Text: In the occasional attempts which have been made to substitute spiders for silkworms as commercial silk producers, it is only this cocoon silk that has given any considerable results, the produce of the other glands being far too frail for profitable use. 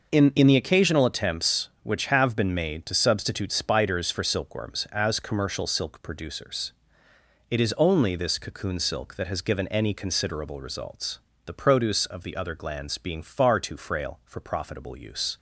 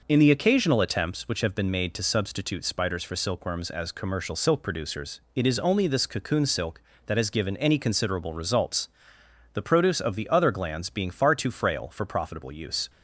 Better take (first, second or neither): second